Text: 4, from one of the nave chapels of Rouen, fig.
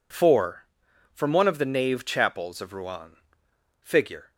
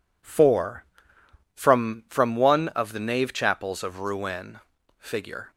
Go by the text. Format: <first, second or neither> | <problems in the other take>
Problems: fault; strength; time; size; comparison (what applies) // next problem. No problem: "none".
first | says "from" twice; at 2.1 s